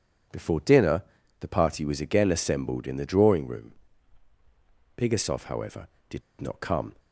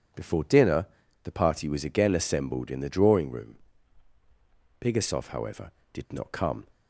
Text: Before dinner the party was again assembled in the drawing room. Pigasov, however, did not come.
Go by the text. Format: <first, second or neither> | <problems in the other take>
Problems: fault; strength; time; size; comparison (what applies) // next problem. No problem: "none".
second | pauses between "dinner" and "the"; at 1.0 s; 0.38 s long; also in the second // pauses between "did" and "not"; slight; at 6.2 s; 0.19 s long